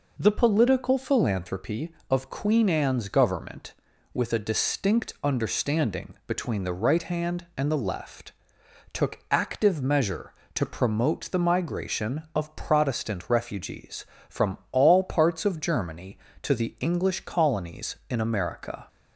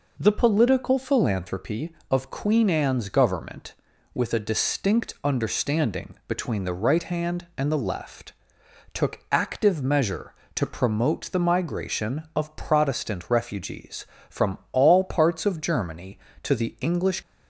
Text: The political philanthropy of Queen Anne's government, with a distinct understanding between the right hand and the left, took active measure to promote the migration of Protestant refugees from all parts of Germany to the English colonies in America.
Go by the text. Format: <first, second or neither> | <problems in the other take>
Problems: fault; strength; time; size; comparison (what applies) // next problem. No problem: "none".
first | stops before "colonies in America"; at 17.2 s